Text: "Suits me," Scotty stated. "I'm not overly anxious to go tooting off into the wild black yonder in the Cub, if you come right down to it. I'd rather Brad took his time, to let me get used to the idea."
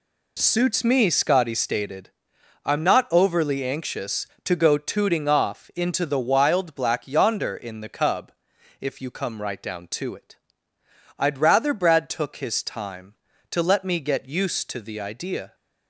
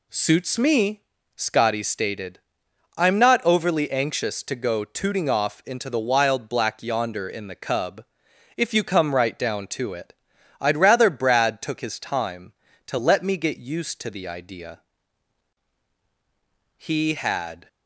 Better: first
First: none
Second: goes on to say "He had"; noticeable; from 16.7 s on; 0.90 s long

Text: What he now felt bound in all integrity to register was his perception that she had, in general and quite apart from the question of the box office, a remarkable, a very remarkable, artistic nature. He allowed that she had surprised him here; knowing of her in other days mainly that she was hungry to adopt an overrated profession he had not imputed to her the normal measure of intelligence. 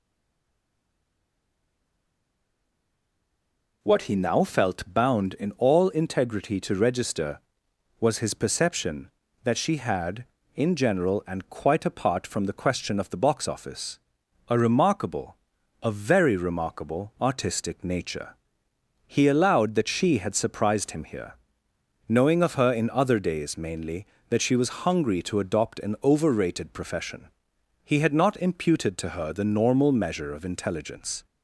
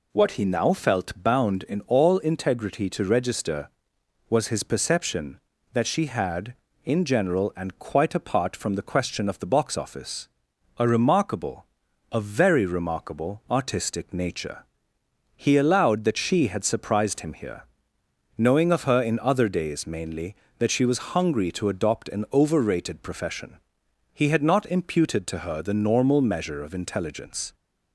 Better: second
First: stays silent before the first word; strong; until 3.8 s; 3.8 s long // pauses between "profession" and "he"; noticeable; at 27.2 s; 0.54 s long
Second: pauses between "profession" and "he"; noticeable; at 23.5 s; 0.54 s long

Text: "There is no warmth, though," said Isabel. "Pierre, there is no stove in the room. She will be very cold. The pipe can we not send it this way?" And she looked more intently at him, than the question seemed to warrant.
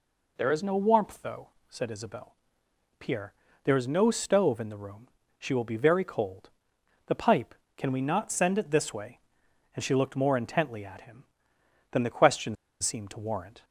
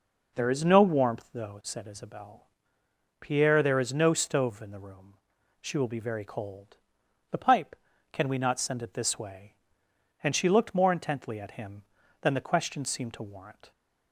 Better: second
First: pauses between "question" and "seemed"; slight; at 12.5 s; 0.25 s long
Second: none

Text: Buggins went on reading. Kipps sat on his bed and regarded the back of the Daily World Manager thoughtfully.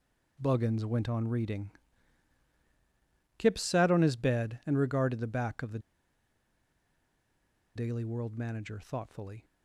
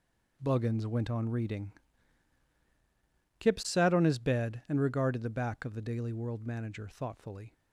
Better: second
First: pauses between "the" and "Daily"; strong; at 5.7 s; 1.9 s long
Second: none

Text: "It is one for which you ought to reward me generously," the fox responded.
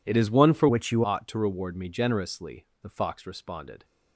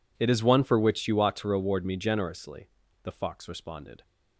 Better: second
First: changes voice from "which" to "you"; from 0.6 to 1.0 s; 0.4 s long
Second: none

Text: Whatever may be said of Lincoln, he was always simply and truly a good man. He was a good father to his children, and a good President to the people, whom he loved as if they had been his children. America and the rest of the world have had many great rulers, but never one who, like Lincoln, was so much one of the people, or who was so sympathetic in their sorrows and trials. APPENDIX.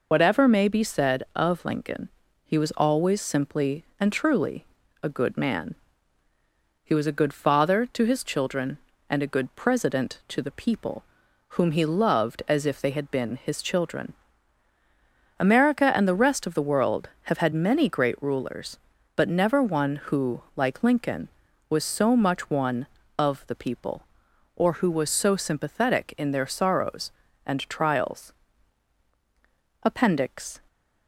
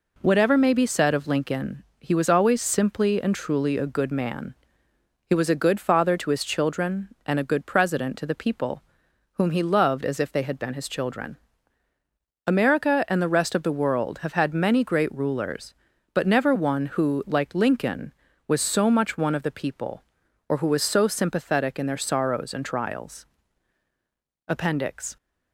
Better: second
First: loses the start of "Whatever"; at 0.1 s; 100 ms // pauses between "truly" and "a"; slight; at 4.6 s; 0.34 s long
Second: none

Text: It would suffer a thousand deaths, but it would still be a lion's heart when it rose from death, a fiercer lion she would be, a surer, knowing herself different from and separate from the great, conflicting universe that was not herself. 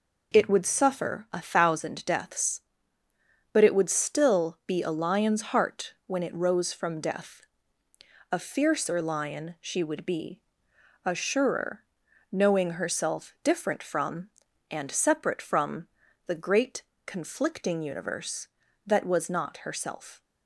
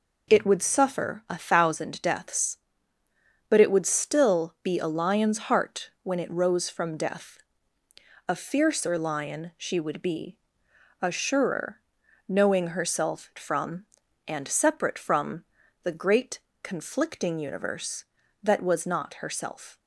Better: first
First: pauses between "from" and "the"; at 15.8 s; 0.40 s long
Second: skips "different"; at 13.3 s // pauses between "from" and "the"; at 15.4 s; 0.40 s long

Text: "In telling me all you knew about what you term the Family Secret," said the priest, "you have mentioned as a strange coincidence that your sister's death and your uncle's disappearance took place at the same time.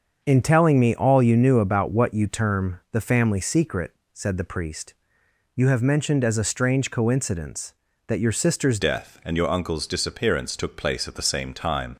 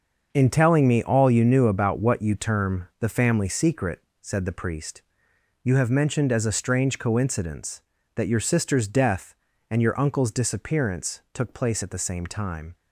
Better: second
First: starts louder than the rest; until 1.2 s; 6.5 dB // changes voice at "death"; from 8.7 s on; 3.2 s long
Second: starts louder than the rest; until 1.3 s; 6.5 dB

